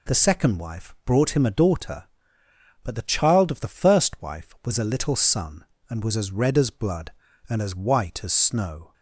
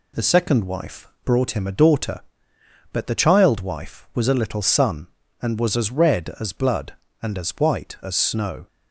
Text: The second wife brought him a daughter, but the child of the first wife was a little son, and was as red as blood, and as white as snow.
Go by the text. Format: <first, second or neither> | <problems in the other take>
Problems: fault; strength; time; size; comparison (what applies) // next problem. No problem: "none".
first | pauses between "wife" and "brought"; slight; at 1.0 s; 0.16 s long // skips "of the first"; at 3.6 s